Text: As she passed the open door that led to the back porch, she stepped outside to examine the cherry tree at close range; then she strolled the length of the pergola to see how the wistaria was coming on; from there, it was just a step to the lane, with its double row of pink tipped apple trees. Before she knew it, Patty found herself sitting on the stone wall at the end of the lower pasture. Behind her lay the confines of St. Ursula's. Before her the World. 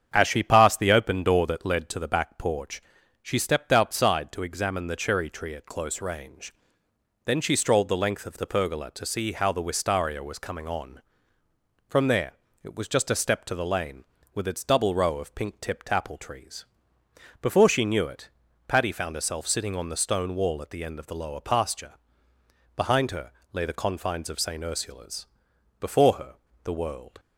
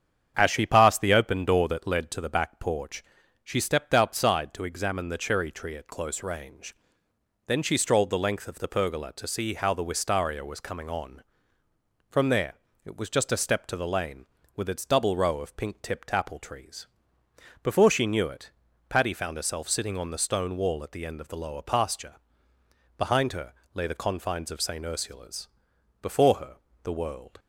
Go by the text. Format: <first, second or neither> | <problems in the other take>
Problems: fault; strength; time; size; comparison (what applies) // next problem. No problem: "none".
neither | starts louder than the rest; strong; the same in both // pauses between "her" and "lay"; slight; the same in both // pauses between "her" and "the"; slight; the same in both